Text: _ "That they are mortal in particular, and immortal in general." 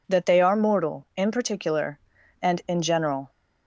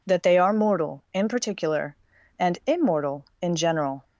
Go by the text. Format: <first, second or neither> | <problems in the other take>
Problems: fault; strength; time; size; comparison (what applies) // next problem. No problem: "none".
second | skips "immortal"; at 2.6 s